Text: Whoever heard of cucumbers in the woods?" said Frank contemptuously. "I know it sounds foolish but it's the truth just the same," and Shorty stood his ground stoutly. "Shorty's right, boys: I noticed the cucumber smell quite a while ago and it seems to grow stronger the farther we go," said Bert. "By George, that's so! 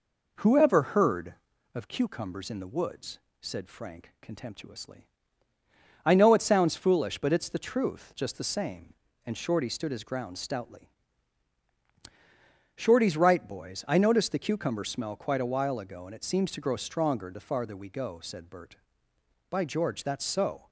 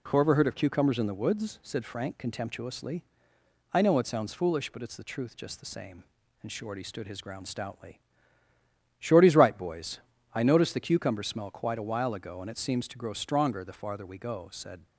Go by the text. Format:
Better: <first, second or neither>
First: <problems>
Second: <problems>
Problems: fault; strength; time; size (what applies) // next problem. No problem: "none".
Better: first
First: none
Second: stops before "Bert By George that's so"; at 14.8 s